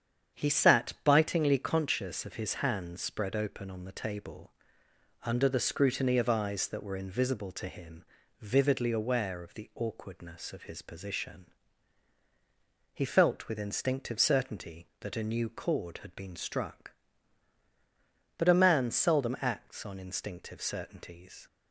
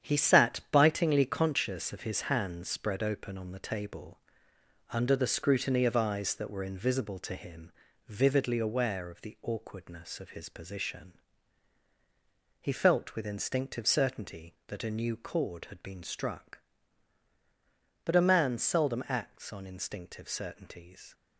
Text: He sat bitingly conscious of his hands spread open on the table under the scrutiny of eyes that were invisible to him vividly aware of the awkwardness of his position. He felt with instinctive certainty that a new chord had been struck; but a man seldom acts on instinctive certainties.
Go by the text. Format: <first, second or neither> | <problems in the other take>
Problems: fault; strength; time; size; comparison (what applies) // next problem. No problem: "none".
first | gets quieter; strong; throughout; 8.5 dB // starts louder than the rest; strong; until 1.1 s; 9 dB; strong in the first // pauses between "table" and "under"; noticeable; at 4.1 s; 0.70 s long; noticeable in the first // pauses between "him" and "vividly"; slight; at 7.7 s; 0.36 s long; slight in the first